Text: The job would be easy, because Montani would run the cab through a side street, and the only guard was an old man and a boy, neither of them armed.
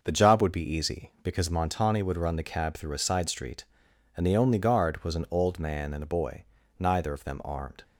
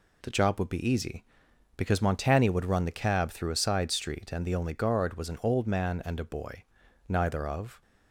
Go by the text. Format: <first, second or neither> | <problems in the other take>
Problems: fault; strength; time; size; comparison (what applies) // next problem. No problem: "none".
first | stops before "them armed"; at 7.8 s